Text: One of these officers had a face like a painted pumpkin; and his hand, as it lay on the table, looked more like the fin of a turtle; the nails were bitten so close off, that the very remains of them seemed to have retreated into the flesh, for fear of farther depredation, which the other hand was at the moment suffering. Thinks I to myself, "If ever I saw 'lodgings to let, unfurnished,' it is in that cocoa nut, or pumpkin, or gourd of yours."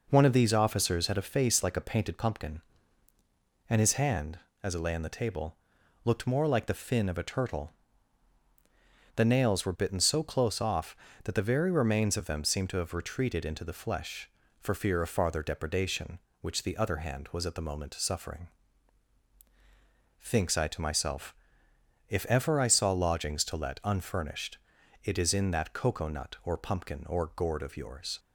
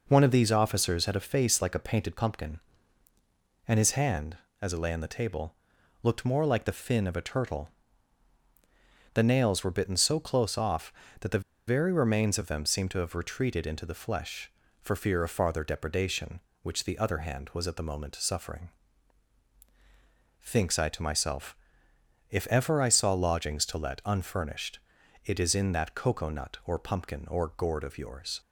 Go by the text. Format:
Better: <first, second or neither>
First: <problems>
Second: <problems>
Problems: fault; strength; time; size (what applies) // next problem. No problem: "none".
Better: first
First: none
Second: pauses between "the" and "very"; slight; at 11.4 s; 0.27 s long